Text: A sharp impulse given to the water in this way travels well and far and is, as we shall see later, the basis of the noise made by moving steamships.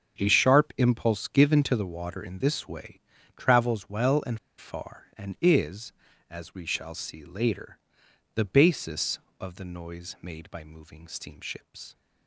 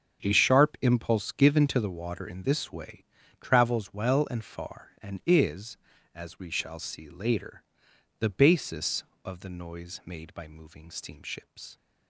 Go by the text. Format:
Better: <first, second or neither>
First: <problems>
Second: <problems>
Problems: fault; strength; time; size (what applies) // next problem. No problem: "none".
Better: second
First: starts louder than the rest; strong; until 1.2 s; 7.5 dB // pauses between "way" and "travels"; slight; at 3.0 s; 0.36 s long // pauses between "and" and "far"; slight; at 4.3 s; 0.21 s long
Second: starts louder than the rest; strong; until 1.2 s; 7.5 dB // pauses between "way" and "travels"; slight; at 3.0 s; 0.36 s long